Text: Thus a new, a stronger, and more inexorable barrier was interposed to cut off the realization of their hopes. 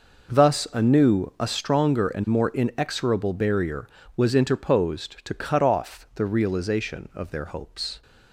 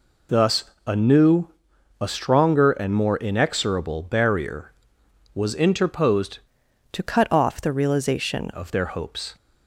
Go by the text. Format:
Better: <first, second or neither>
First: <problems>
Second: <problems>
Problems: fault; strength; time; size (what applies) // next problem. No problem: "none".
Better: first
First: none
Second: pauses between "Thus" and "a"; slight; at 0.6 s; 0.24 s long // changes voice from "to" to "realization"; from 6.9 to 8.5 s; 1.6 s long